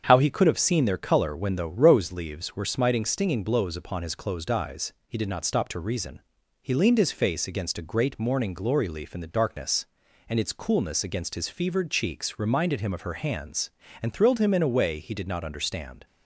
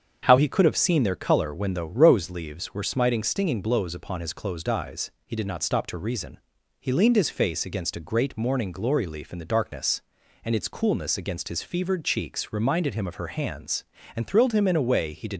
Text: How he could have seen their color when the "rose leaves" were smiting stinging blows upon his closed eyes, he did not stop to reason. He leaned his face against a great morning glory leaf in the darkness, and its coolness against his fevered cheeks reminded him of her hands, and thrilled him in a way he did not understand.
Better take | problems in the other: first | starts louder than the rest; strong; until 1.2 s; 7.5 dB; strong in the first // stops before "not understand"; at 15.3 s

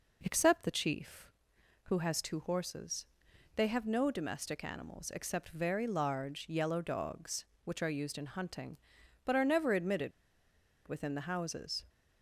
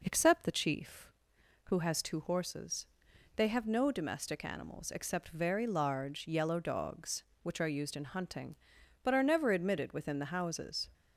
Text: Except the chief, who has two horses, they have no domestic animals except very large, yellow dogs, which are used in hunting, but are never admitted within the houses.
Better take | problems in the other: second | pauses between "admitted" and "within"; noticeable; at 10.1 s; 0.76 s long

